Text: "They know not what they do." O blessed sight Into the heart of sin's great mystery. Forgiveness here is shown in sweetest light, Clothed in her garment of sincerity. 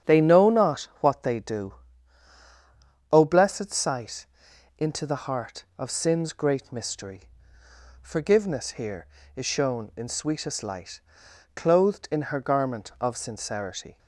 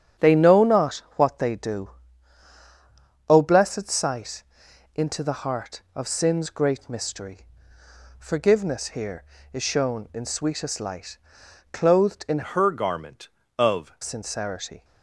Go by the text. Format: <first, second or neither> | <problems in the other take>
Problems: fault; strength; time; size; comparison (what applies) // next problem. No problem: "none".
first | starts louder than the rest; strong; until 1.3 s; 9 dB; strong in the first // pauses between "sight" and "Into"; noticeable; at 4.4 s; 0.54 s long; noticeable in the first // changes voice from "her" to "of"; from 12.4 to 13.9 s; 1.5 s long